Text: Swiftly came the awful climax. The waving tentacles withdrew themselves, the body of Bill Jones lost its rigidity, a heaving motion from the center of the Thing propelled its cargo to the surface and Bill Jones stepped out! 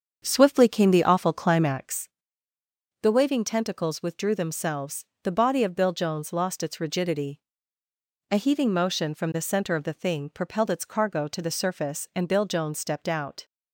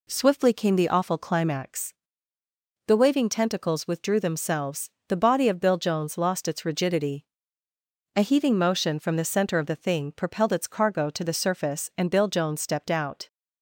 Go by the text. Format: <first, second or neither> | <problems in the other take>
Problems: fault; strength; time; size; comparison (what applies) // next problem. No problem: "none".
second | starts louder than the rest; strong; until 2.1 s; 7 dB